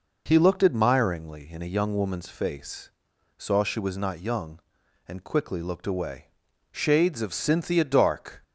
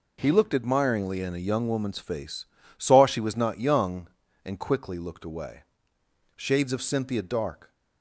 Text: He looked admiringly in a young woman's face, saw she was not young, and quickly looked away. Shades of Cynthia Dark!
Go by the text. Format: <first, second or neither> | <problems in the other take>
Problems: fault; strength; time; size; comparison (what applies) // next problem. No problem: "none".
neither | none